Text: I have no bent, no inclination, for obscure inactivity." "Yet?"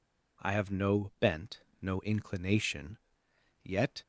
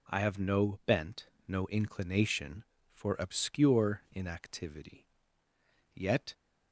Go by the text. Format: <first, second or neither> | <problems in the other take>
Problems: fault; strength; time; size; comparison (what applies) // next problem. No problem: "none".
second | skips "for obscure inactivity"; at 3.2 s